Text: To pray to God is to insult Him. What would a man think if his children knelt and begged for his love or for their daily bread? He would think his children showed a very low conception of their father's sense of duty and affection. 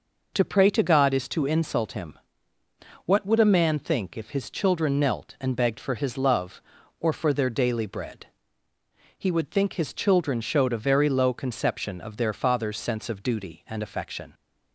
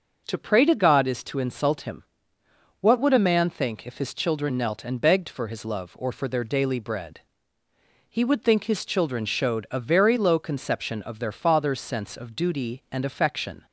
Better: neither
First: none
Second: none

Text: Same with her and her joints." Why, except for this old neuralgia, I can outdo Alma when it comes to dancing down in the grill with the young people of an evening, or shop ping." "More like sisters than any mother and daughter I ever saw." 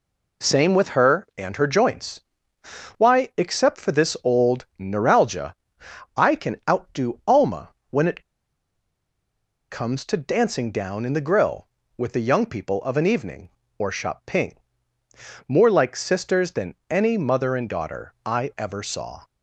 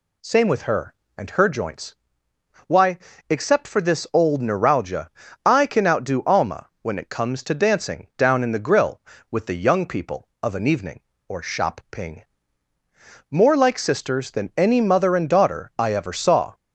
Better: second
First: pauses between "Alma" and "when"; slight; at 7.7 s; 0.18 s long // pauses between "it" and "comes"; strong; at 8.2 s; 1.4 s long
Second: none

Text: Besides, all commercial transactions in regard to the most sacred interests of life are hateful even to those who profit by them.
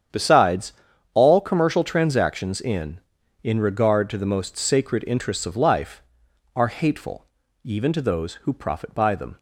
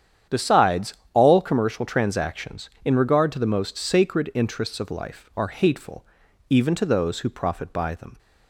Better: second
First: starts louder than the rest; strong; until 1.5 s; 8.5 dB // says "in" twice; at 3.4 s // pauses between "hateful" and "even"; at 7.2 s; 0.38 s long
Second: starts louder than the rest; strong; until 1.5 s; 9 dB // pauses between "hateful" and "even"; noticeable; at 6.0 s; 0.46 s long

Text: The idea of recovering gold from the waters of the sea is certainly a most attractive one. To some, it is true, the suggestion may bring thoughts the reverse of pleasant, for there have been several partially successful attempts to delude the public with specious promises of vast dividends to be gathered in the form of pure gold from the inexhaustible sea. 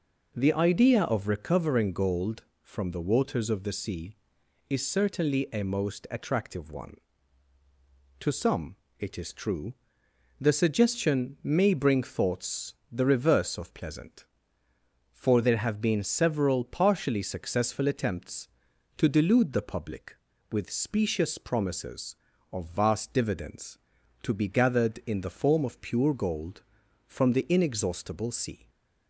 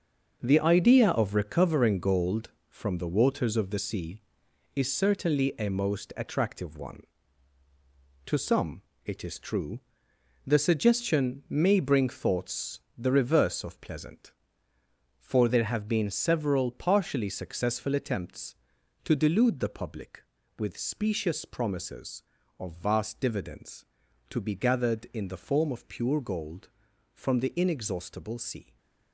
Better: first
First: pauses between "thoughts" and "the"; slight; at 12.7 s; 0.18 s long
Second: gets quieter; strong; throughout; 8.5 dB // pauses between "thoughts" and "the"; slight; at 12.8 s; 0.18 s long

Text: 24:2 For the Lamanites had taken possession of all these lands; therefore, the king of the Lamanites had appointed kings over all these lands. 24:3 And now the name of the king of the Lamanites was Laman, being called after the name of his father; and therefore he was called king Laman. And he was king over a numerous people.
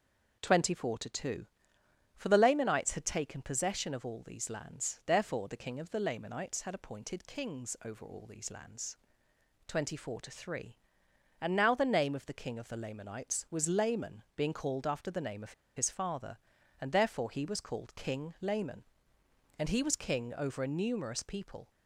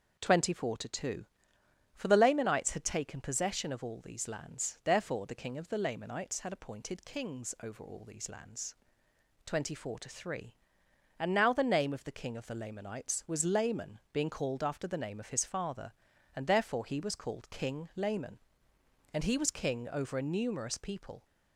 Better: second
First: pauses between "of" and "his"; slight; at 15.5 s; 0.23 s long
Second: none

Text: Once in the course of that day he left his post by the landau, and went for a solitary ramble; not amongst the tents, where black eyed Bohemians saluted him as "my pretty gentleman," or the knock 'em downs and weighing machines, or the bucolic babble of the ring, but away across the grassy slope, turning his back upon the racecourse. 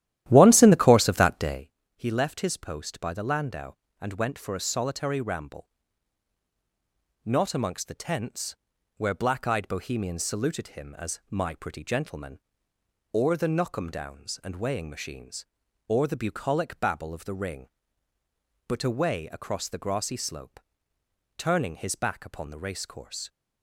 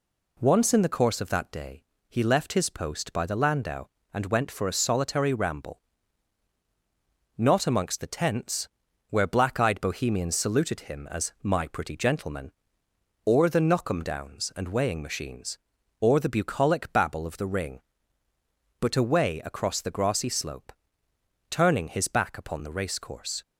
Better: second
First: starts louder than the rest; strong; until 1.7 s; 13 dB // pauses between "day" and "he"; slight; at 1.6 s; 0.26 s long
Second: pauses between "day" and "he"; slight; at 1.8 s; 0.26 s long

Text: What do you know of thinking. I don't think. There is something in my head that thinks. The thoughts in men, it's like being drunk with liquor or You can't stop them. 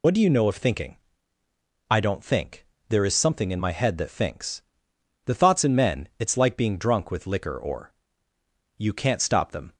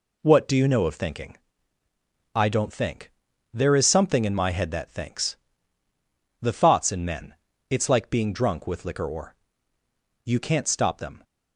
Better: second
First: loses the start of "What"; at 0.0 s; 60 ms // pauses between "or" and "You"; noticeable; at 7.9 s; 0.84 s long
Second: pauses between "or" and "You"; noticeable; at 9.3 s; 0.90 s long

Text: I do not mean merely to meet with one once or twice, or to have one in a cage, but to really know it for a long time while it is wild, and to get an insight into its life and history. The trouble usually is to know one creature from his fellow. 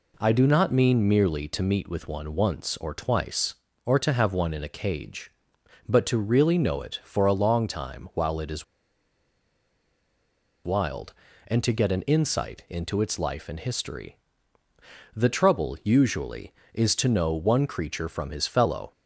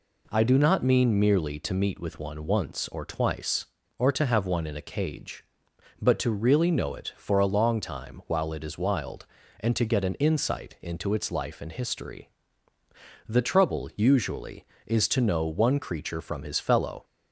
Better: second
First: pauses between "is" and "wild"; strong; at 8.6 s; 2.0 s long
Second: none

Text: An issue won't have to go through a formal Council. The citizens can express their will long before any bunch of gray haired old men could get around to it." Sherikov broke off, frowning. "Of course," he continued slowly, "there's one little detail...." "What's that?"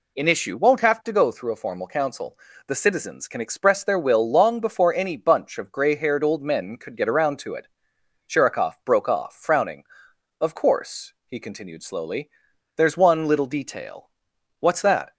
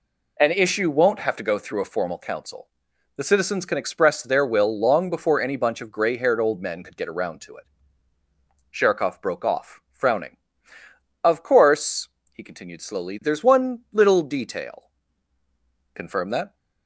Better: first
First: none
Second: says "Confirm" for "What's"; at 15.9 s

